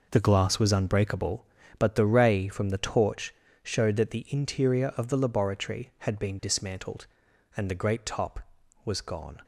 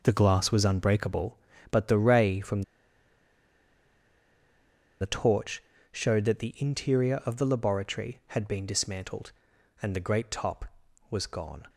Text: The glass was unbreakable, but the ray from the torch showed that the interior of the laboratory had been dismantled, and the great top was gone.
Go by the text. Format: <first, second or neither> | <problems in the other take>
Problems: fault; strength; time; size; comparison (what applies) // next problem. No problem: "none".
first | pauses between "from" and "the"; strong; at 2.6 s; 2.3 s long // pauses between "torch" and "showed"; slight; at 5.6 s; 0.28 s long; slight in the first